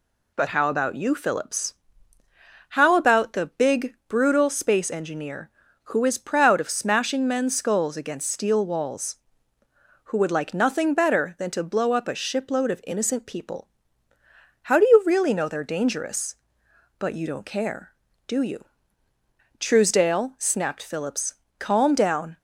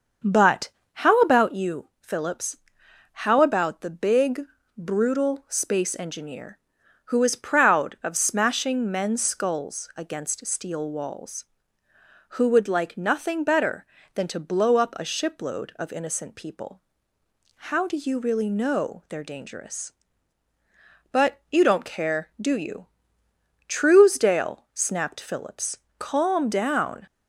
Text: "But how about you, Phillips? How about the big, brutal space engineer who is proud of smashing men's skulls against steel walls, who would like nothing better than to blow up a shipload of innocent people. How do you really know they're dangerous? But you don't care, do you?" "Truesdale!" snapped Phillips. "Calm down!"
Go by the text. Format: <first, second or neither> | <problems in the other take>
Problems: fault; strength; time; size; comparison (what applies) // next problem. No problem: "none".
first | starts louder than the rest; until 1.5 s; 6.5 dB // pauses between "But" and "how"; slight; at 0.6 s; 0.26 s long